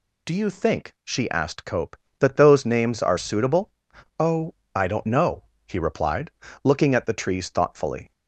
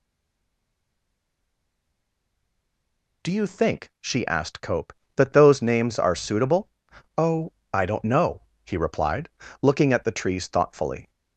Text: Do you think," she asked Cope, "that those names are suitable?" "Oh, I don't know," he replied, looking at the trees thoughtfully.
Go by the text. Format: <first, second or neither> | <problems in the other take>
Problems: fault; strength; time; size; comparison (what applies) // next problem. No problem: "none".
first | stays silent before the first word; strong; until 3.2 s; 3.2 s long